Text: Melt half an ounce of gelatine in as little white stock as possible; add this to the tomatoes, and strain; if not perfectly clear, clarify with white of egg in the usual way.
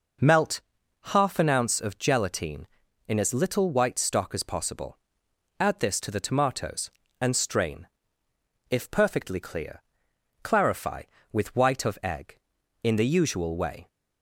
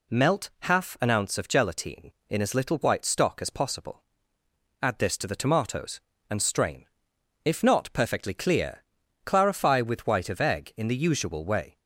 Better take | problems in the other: second | pauses between "Melt" and "half"; noticeable; at 0.5 s; 0.54 s long // skips "not"; at 8.9 s

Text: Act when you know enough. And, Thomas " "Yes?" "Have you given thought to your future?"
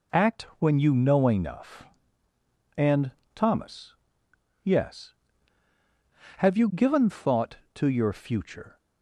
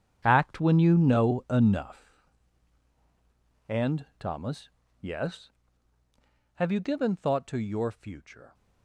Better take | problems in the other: first | gets quieter; strong; throughout; 13 dB

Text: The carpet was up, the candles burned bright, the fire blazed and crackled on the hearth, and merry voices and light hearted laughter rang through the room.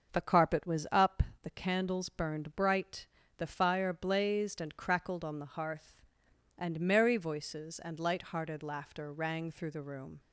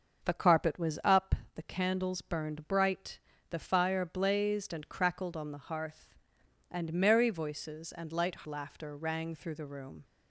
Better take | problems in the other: first | starts louder than the rest; until 1.2 s; 6.5 dB; also in the first // skips "hearted"; at 8.4 s

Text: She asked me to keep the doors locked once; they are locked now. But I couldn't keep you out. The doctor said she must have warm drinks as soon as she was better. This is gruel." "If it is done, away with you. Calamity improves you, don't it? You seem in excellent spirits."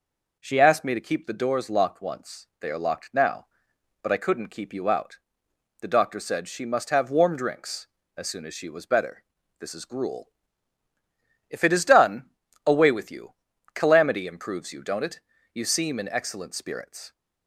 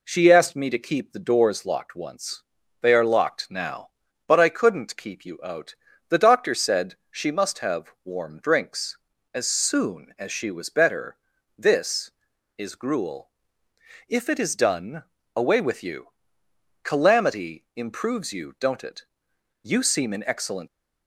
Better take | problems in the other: first | pauses between "said" and "she"; slight; at 6.9 s; 0.16 s long // stops before "spirits"; at 20.6 s

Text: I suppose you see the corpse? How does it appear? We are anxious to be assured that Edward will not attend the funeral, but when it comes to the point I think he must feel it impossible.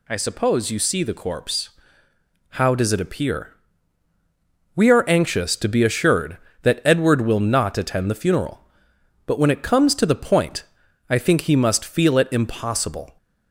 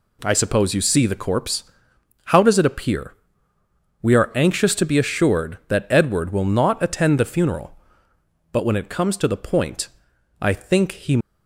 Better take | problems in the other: first | pauses between "point" and "I"; noticeable; at 9.8 s; 0.54 s long; noticeable in the first // stops before "must feel it impossible"; at 11.1 s

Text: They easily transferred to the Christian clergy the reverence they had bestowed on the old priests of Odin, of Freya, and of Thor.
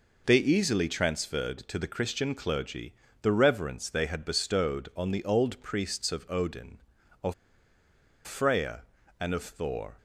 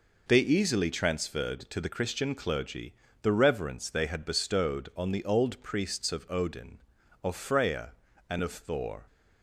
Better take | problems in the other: second | pauses between "clergy" and "the"; slight; at 2.9 s; 0.26 s long; slight in the second // pauses between "of" and "Freya"; noticeable; at 7.3 s; 0.92 s long

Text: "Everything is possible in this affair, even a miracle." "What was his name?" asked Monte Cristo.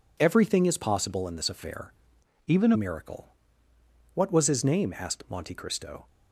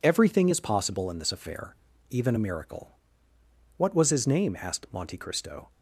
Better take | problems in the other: second | changes voice from "even" to "a"; from 2.4 to 2.7 s; 0.3 s long

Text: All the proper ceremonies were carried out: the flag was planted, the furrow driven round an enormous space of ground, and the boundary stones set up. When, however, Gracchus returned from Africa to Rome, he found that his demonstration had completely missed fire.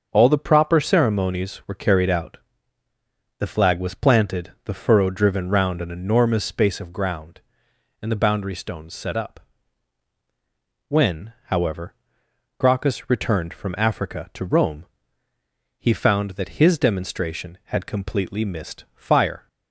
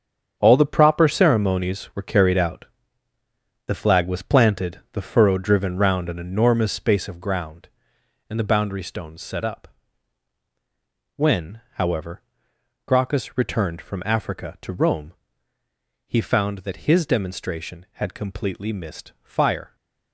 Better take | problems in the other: first | gets quieter; strong; throughout; 10.5 dB // starts louder than the rest; strong; until 1.3 s; 8 dB; also in the first

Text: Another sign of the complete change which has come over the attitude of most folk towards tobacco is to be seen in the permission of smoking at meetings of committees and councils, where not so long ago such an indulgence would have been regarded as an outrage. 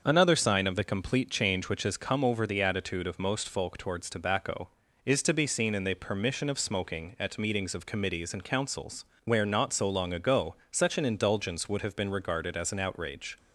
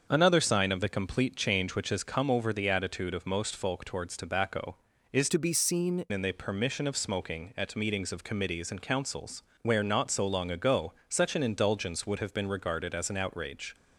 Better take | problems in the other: first | starts louder than the rest; until 1.1 s; 6.5 dB; also in the first // changes voice from "to" to "seen"; from 5.2 to 6.0 s; 0.8 s long // pauses between "ago" and "such"; slight; at 10.9 s; 0.16 s long; slight in the first

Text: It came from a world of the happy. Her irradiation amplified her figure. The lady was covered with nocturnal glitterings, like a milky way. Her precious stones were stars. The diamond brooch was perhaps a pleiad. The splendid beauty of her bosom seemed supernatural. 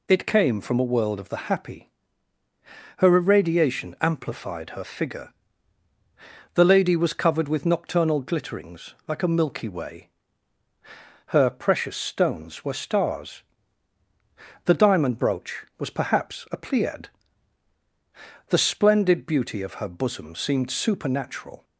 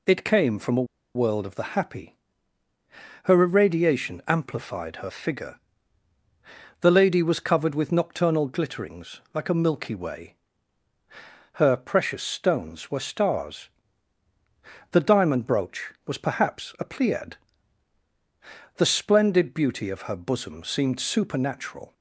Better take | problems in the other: first | pauses between "a" and "world"; slight; at 0.8 s; 0.30 s long

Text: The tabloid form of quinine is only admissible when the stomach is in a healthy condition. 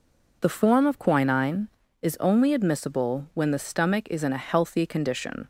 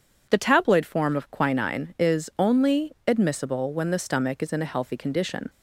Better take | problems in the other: second | skips "tabloid"; at 0.4 s

